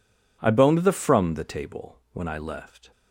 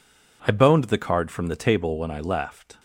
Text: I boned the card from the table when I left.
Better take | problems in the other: second | skips "card"; at 0.9 s

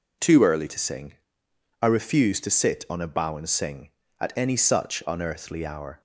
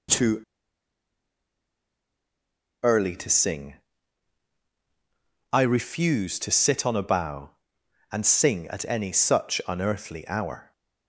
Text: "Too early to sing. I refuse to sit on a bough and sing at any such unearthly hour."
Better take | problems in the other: first | pauses between "Too" and "early"; strong; at 0.4 s; 2.4 s long

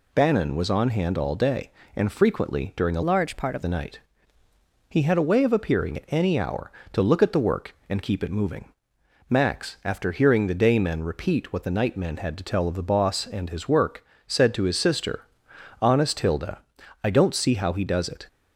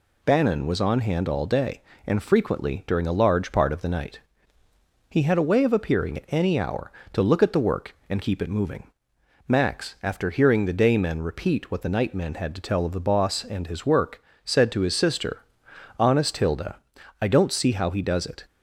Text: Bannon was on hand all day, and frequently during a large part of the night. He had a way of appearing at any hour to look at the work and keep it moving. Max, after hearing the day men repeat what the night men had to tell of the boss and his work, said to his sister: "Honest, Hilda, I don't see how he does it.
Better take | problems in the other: second | changes voice from "large" to "of"; from 3.0 to 3.6 s; 0.6 s long

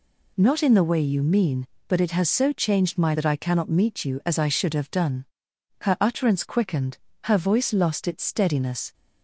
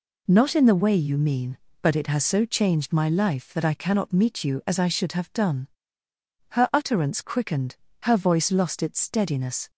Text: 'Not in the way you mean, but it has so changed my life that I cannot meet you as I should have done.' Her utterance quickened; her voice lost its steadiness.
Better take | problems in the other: second | skips "life"; at 3.1 s

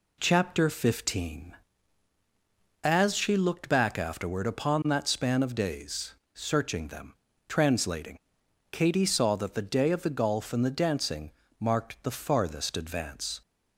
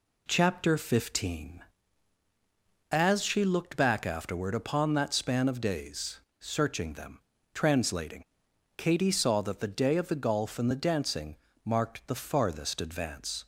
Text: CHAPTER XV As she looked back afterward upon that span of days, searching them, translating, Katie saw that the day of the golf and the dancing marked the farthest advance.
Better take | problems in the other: neither | pauses between "dancing" and "marked"; slight; the same in both

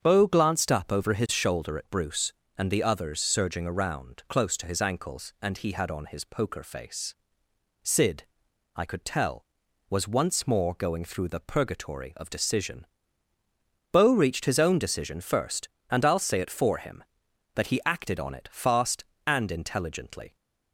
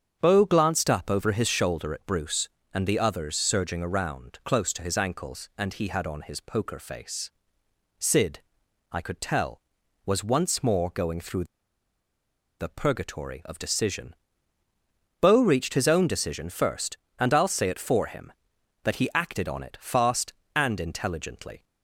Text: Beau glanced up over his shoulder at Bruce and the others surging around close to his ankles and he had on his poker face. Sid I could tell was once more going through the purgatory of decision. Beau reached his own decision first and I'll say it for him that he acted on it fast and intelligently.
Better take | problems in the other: first | starts louder than the rest; strong; until 1.2 s; 7.5 dB; strong in the first // pauses between "Sid" and "I"; noticeable; at 8.4 s; 0.50 s long; noticeable in the first // pauses between "through" and "the"; at 11.4 s; 1.1 s long

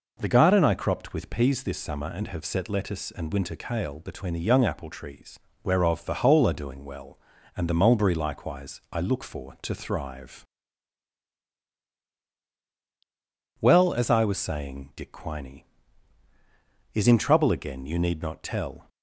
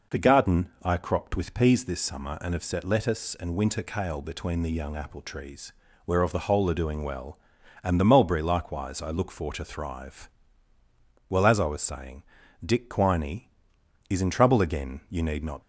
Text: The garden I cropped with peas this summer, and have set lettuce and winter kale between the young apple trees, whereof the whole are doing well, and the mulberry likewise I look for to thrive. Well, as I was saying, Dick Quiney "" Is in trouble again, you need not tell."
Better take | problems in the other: first | stops before "tell"; at 15.6 s

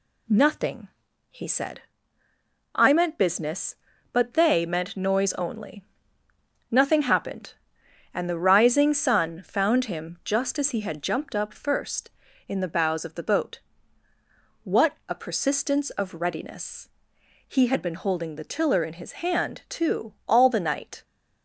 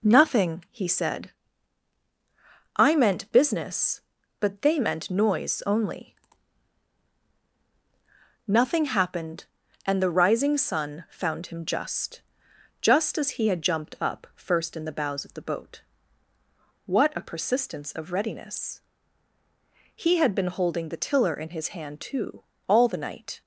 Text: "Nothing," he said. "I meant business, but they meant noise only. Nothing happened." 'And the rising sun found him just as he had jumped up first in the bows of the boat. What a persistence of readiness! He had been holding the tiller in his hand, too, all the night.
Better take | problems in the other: first | says "just" twice; at 12.8 s

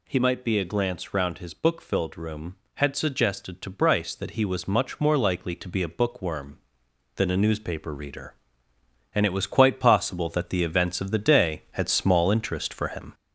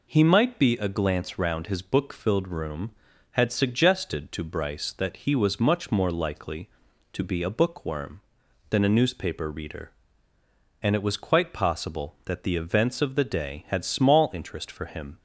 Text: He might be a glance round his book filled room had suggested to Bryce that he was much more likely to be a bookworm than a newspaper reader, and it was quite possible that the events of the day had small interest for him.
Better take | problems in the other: second | gets louder; noticeable; throughout; 4.5 dB

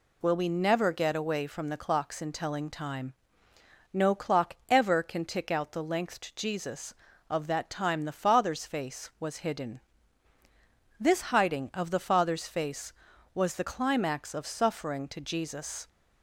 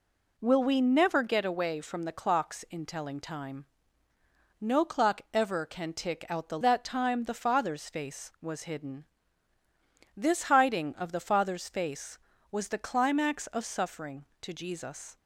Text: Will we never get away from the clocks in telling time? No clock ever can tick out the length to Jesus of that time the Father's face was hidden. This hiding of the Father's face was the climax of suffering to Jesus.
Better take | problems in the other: first | skips "length to Jesus of"; at 6.5 s

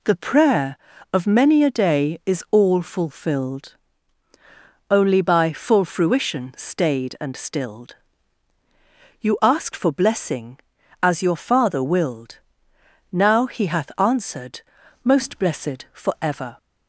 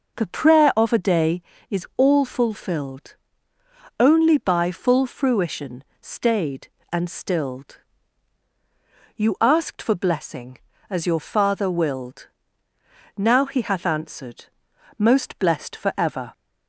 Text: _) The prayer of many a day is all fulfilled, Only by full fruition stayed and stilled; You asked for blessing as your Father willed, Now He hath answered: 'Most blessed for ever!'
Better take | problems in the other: first | skips "many"; at 0.9 s // pauses between "fruition" and "stayed"; slight; at 5.8 s; 0.18 s long

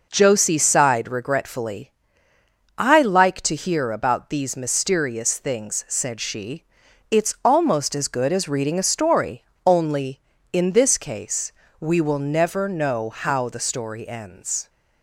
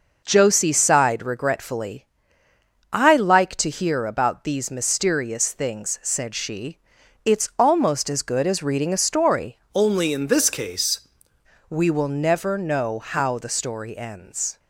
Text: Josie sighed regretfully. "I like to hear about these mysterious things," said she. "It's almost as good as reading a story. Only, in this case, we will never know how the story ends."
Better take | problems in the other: first | changes voice from "Only" to "case"; from 9.7 to 10.9 s; 1.2 s long

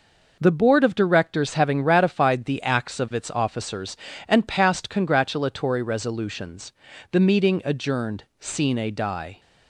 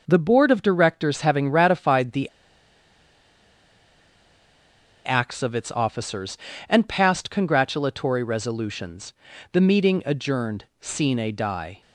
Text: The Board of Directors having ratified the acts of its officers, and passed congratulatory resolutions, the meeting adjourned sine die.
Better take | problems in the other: first | pauses between "the" and "acts"; strong; at 2.2 s; 2.7 s long // pauses between "adjourned" and "sine"; slight; at 10.6 s; 0.16 s long; slight in the first

